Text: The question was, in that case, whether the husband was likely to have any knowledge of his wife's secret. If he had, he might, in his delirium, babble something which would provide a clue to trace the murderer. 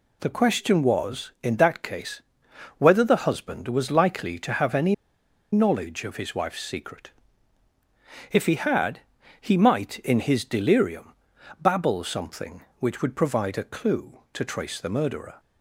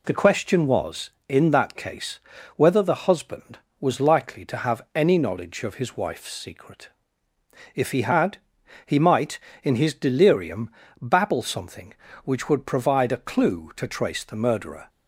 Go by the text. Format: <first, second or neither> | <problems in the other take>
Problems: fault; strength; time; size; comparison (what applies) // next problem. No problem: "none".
second | pauses between "any" and "knowledge"; noticeable; at 4.9 s; 0.58 s long